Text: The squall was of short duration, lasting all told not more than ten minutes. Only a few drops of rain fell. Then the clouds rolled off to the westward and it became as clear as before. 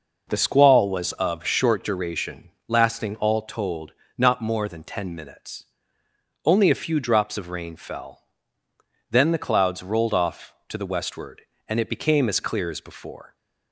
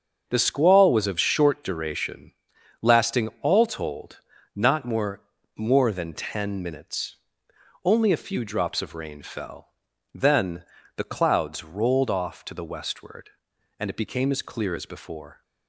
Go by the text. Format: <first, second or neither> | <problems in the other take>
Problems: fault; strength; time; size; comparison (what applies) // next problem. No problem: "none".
first | starts louder than the rest; until 1.2 s; 6.5 dB // pauses between "told" and "not"; slight; at 4.1 s; 0.36 s long; slight in the first // says "more" twice; at 5.5 s // pauses between "Then" and "the"; slight; at 10.6 s; 0.32 s long